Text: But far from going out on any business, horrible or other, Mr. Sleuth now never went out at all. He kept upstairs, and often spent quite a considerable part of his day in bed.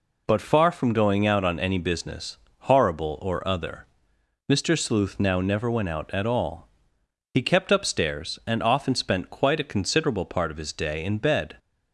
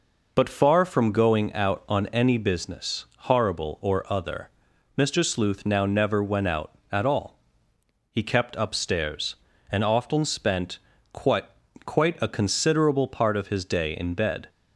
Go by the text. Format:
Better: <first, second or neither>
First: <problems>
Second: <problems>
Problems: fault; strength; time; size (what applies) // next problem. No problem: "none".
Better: first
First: none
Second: pauses between "spent" and "quite"; slight; at 10.7 s; 0.34 s long // says "quite" twice; at 11.8 s